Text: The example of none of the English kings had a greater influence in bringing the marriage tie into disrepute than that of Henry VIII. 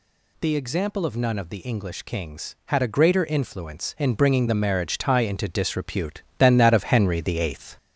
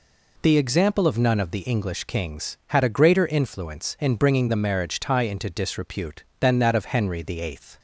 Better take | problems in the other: second | gets louder; throughout; 3.5 dB

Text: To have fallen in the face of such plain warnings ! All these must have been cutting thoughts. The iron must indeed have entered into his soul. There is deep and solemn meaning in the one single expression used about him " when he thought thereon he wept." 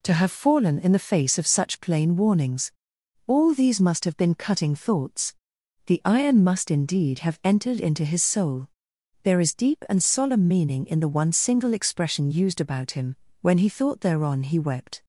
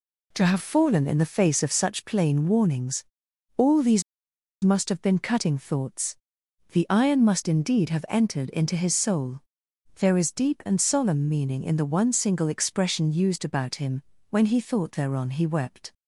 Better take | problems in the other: first | pauses between "these" and "must"; noticeable; at 4.0 s; 0.62 s long

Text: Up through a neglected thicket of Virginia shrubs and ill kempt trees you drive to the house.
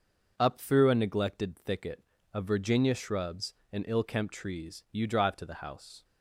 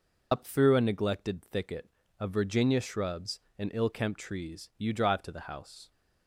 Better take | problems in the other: first | loses the start of "Up"; at 0.3 s; 75 ms

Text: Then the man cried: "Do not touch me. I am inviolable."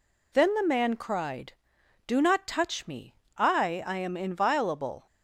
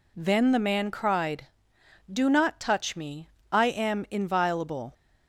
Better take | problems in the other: second | says "I" twice; at 3.8 s

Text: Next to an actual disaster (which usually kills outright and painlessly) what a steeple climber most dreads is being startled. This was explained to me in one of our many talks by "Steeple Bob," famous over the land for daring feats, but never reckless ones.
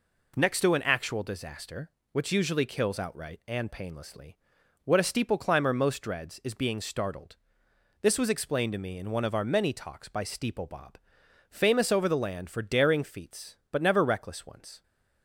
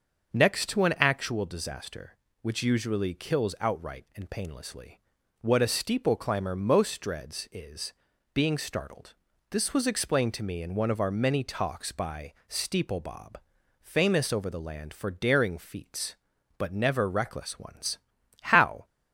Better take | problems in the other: first | starts louder than the rest; until 1.3 s; 6.5 dB // pauses between "is" and "being"; at 7.9 s; 0.42 s long // pauses between "by" and "Steeple"; slight; at 12.3 s; 0.16 s long // goes on to say "How"; slight; from 18.3 s on; 0.46 s long

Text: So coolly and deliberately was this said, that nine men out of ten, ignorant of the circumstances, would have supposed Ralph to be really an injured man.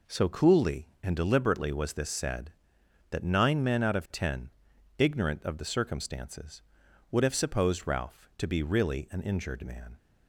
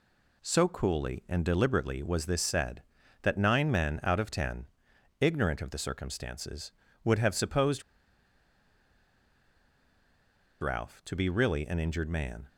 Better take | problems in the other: first | pauses between "supposed" and "Ralph"; strong; at 7.8 s; 2.7 s long

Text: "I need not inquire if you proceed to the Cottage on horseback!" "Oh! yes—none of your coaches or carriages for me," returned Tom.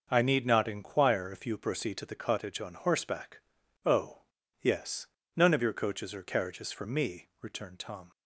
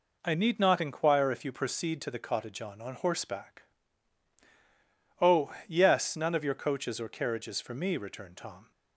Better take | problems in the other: first | says "on" twice; at 2.8 s

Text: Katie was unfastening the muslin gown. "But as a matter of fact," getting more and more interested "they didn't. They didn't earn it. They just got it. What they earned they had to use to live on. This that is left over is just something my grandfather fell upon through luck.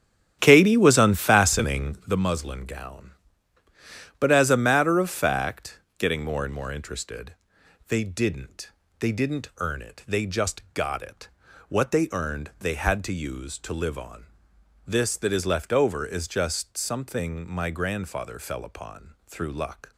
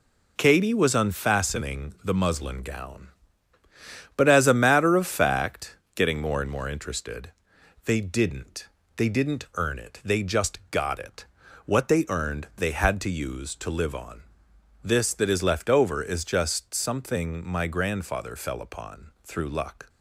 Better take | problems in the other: second | starts louder than the rest; strong; until 2.3 s; 10 dB // pauses between "interested" and "they"; noticeable; at 7.3 s; 0.56 s long; noticeable in the second

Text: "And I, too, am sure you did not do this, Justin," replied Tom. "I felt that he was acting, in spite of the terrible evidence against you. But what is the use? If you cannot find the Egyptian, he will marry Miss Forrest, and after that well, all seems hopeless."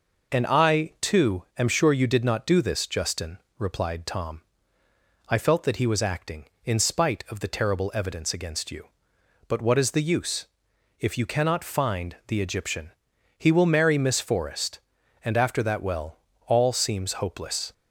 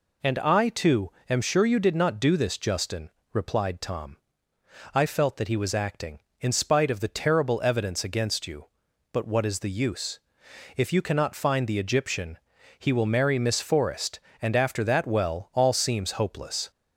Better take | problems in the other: neither | none

